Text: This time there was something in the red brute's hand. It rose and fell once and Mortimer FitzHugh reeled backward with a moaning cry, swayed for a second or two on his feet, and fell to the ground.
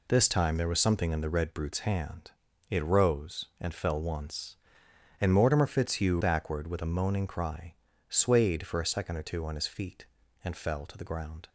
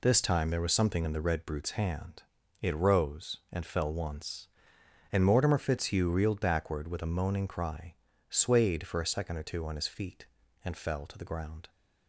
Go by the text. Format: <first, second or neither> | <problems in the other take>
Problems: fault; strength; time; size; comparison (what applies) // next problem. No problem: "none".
second | skips "reeled"; at 6.2 s